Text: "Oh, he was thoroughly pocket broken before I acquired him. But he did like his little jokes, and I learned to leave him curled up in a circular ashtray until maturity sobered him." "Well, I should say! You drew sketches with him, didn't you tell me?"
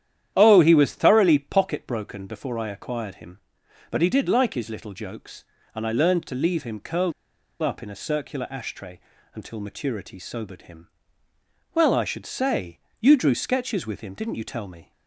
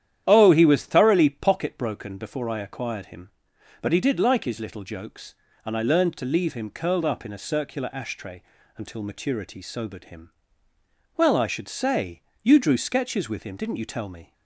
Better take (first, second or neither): second